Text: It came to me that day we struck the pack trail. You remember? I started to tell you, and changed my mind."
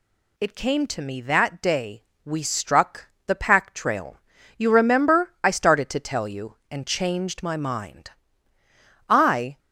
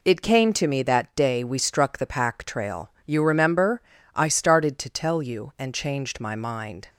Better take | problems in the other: second | pauses between "day" and "we"; slight; at 2.0 s; 0.22 s long // pauses between "struck" and "the"; slight; at 3.0 s; 0.18 s long // goes on to say "I"; from 9.0 s on; 0.50 s long

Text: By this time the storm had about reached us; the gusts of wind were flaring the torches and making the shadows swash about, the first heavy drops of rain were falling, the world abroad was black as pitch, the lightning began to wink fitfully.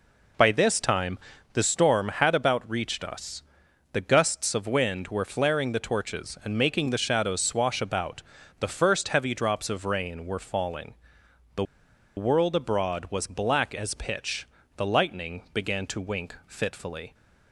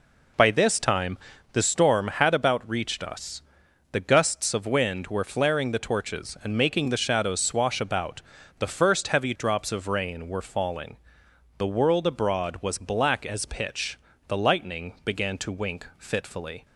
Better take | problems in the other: second | pauses between "time" and "the"; slight; at 1.1 s; 0.34 s long; slight in the second // pauses between "the" and "world"; noticeable; at 11.6 s; 0.52 s long

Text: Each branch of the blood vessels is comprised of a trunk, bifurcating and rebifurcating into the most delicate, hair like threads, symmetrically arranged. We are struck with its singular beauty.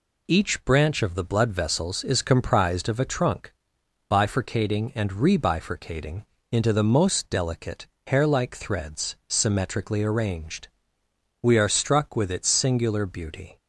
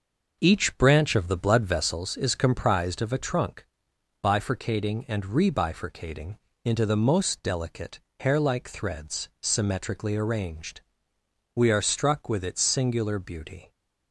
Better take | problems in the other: first | starts louder than the rest; noticeable; until 2.0 s; 6 dB // pauses between "rebifurcating" and "into"; slight; at 6.3 s; 0.26 s long; slight in the first

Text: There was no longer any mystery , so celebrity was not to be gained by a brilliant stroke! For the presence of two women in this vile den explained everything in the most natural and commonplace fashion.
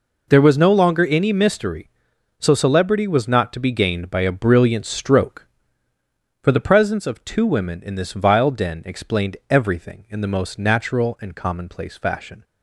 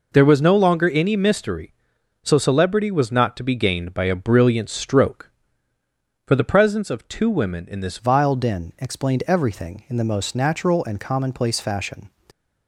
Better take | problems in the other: first | changes voice at "vile"; from 7.9 s on; 4.1 s long

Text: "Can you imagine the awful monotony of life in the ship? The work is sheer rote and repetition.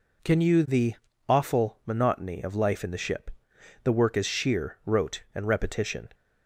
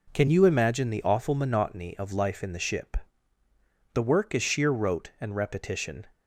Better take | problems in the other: second | skips "imagine"; at 0.6 s // pauses between "the" and "awful"; slight; at 0.9 s; 0.34 s long

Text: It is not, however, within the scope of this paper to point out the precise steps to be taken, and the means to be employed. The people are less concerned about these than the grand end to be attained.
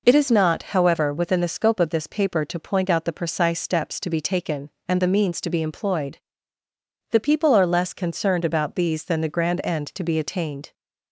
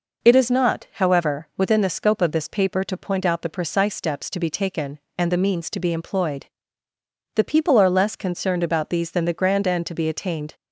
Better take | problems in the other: neither | none

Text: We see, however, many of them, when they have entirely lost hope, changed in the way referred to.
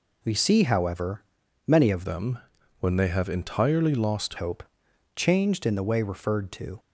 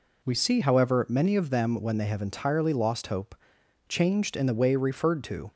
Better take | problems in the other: second | changes voice from "them" to "lost"; from 2.0 to 4.3 s; 2.3 s long

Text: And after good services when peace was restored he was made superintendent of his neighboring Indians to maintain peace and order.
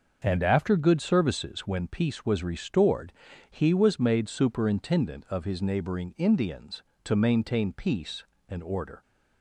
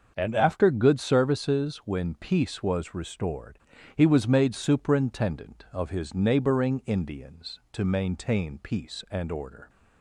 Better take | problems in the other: neither | starts louder than the rest; the same in both // pauses between "restored" and "he"; the same in both

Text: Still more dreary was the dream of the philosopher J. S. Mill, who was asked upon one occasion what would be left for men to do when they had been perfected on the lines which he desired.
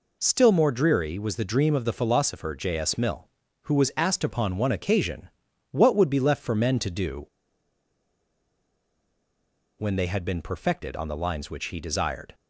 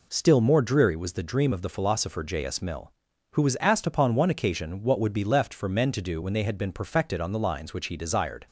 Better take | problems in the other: second | pauses between "occasion" and "what"; at 5.2 s; 0.44 s long // pauses between "do" and "when"; strong; at 7.2 s; 2.5 s long

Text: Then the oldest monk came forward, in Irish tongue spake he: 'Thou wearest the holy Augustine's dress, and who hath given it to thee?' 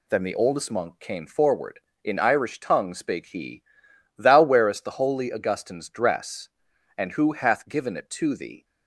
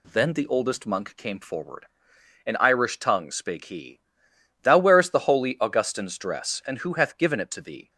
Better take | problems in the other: neither | none

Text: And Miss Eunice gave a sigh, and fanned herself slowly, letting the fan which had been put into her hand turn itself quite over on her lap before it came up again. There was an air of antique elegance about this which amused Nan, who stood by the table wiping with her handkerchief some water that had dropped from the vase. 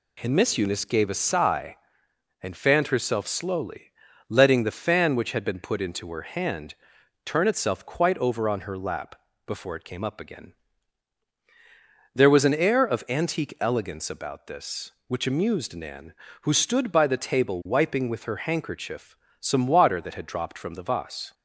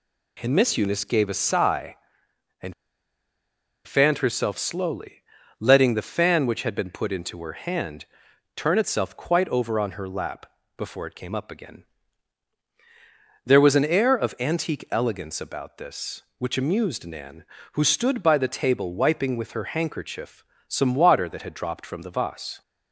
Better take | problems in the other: first | pauses between "and" and "fanned"; at 2.7 s; 1.1 s long // pauses between "hand" and "turn"; noticeable; at 8.0 s; 0.50 s long; noticeable in the first // pauses between "lap" and "before"; slight; at 10.4 s; 0.32 s long; slight in the first // pauses between "handkerchief" and "some"; slight; at 20.4 s; 0.24 s long; slight in the first

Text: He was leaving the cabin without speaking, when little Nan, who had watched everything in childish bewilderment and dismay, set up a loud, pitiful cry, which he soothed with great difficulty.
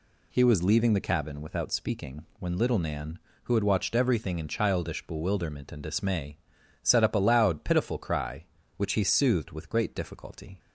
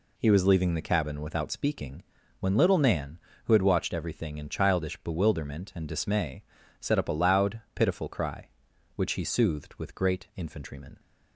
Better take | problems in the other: first | says "infantrymen" for "difficulty"; at 10.3 s

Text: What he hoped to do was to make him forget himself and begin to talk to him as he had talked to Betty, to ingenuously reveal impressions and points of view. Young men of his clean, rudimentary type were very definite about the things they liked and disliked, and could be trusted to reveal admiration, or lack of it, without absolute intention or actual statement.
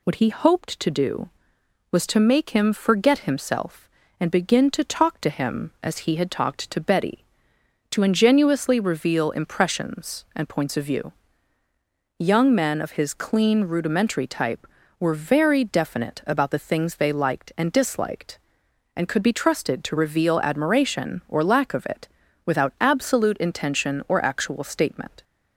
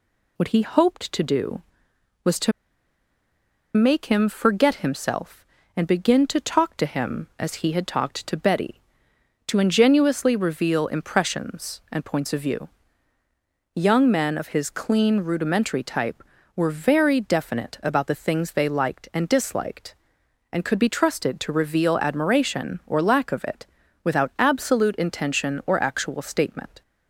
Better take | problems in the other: first | pauses between "to" and "make"; at 2.5 s; 1.2 s long

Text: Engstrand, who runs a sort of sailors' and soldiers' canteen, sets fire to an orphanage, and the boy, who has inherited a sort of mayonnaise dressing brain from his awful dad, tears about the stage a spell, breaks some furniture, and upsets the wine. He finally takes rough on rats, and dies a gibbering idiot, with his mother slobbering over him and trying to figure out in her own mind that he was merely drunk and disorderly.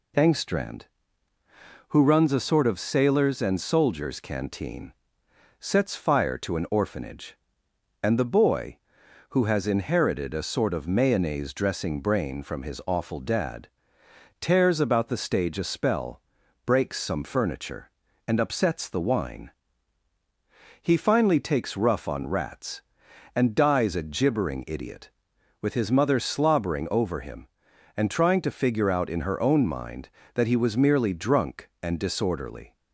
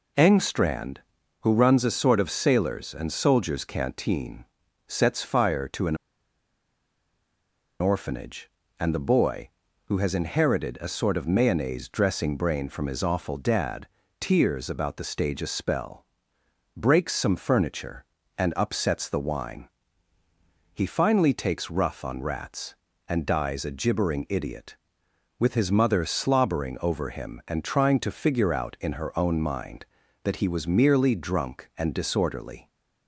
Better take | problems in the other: first | pauses between "an" and "orphanage"; strong; at 5.9 s; 1.8 s long

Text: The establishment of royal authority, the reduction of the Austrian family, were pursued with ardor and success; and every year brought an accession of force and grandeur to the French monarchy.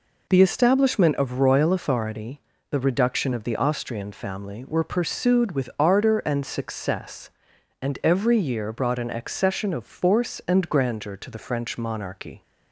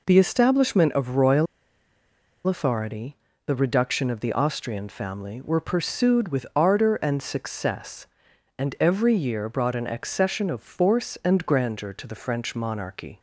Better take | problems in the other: first | pauses between "royal" and "authority"; at 1.4 s; 1.0 s long

